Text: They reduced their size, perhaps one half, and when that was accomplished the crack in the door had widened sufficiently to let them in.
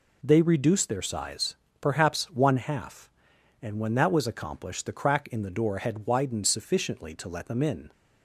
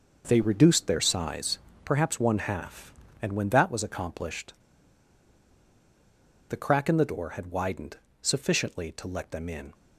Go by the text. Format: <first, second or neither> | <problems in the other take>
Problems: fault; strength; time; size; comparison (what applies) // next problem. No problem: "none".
first | pauses between "accomplished" and "the"; strong; at 4.5 s; 1.9 s long // pauses between "widened" and "sufficiently"; slight; at 7.9 s; 0.24 s long